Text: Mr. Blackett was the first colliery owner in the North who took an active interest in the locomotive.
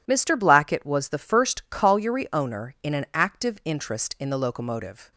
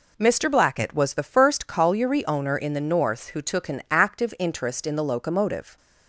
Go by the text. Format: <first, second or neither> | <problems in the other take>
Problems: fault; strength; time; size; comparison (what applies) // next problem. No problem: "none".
second | skips "the North who took"; at 2.9 s